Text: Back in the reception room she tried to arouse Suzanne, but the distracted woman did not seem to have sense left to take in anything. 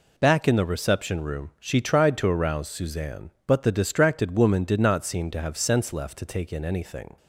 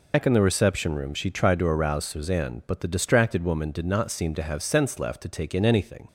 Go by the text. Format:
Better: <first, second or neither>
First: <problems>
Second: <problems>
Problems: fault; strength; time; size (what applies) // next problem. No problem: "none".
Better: first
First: none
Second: loses the start of "Back"; at 0.1 s; 90 ms